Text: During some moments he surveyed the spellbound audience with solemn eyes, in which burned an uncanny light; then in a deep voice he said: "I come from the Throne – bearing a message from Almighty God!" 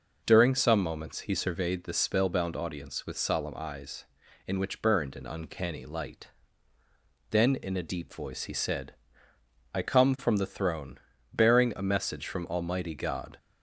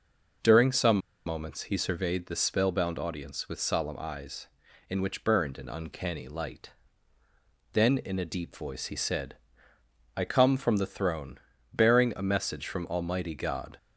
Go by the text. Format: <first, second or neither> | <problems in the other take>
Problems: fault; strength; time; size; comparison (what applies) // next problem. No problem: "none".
first | pauses between "some" and "moments"; slight; at 0.9 s; 0.28 s long